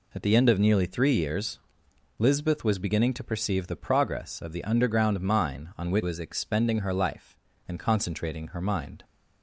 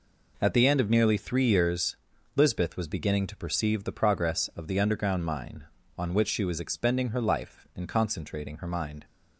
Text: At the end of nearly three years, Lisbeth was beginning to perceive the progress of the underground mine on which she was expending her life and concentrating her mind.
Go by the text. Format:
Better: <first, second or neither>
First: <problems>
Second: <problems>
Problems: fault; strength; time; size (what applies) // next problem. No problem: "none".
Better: second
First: skips "she"; at 6.0 s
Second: none